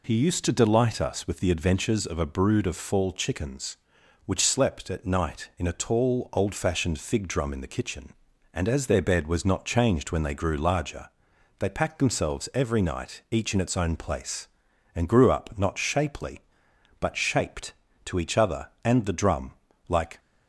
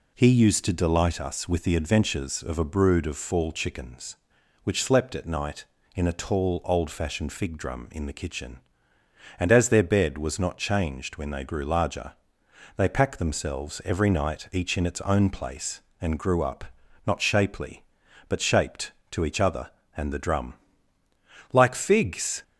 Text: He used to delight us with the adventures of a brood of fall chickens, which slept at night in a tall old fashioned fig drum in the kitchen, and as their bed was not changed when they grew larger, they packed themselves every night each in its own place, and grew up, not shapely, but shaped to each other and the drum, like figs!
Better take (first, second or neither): second